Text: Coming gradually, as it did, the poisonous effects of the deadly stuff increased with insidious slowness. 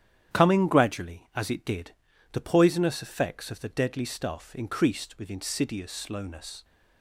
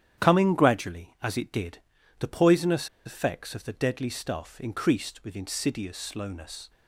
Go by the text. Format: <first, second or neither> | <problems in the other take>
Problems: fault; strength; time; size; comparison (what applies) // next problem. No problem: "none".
first | starts louder than the rest; strong; until 1.2 s; 10 dB; strong in the first // pauses between "poisonous" and "effects"; slight; at 2.8 s; 0.17 s long